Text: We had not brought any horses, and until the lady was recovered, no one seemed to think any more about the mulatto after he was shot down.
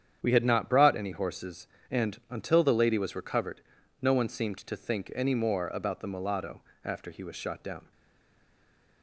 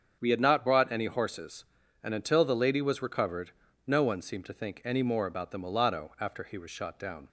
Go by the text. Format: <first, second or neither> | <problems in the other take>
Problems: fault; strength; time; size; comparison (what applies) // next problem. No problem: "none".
second | starts louder than the rest; strong; until 1.2 s; 8.5 dB; strong in the second // pauses between "mulatto" and "after"; slight; at 6.6 s; 0.24 s long // stays silent after the last word; noticeable; from 7.9 s on; 1.1 s long